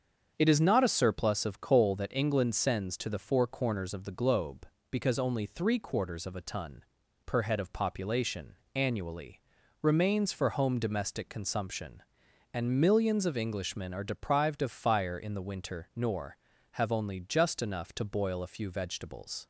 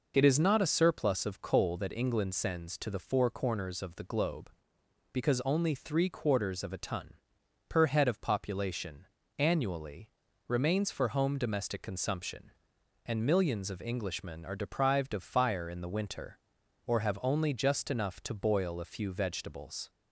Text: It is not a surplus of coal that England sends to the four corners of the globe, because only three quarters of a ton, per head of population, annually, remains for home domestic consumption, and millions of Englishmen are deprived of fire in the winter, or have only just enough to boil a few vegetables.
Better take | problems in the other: second | starts louder than the rest; until 1.3 s; 7 dB // says "nor" for "or"; at 15.9 s

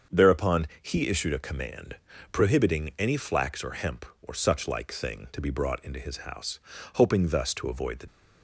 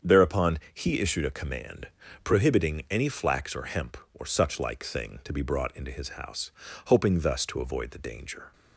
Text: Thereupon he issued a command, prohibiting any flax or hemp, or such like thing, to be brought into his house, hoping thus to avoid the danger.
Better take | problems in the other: second | starts louder than the rest; until 1.2 s; 6.5 dB; strong in the second // stops before "danger"; at 8.0 s

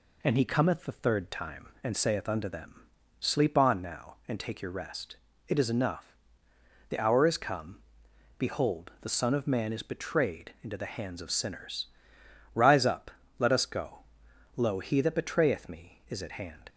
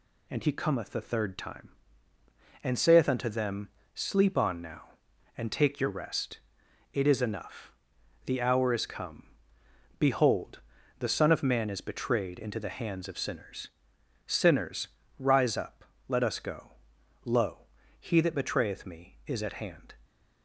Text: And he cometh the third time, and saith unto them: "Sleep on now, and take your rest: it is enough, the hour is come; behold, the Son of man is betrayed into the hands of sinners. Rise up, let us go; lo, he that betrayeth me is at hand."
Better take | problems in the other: first | says "sinners" twice; at 14.2 s

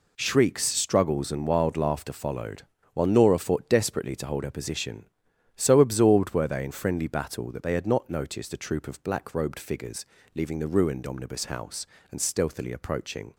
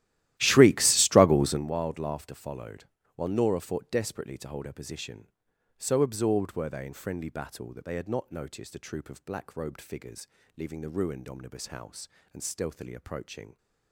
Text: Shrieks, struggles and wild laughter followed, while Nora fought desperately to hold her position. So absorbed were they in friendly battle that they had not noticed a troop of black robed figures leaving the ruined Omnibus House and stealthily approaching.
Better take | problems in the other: first | starts louder than the rest; strong; until 1.7 s; 14.5 dB // pauses between "figures" and "leaving"; slight; at 10.2 s; 0.28 s long; slight in the first

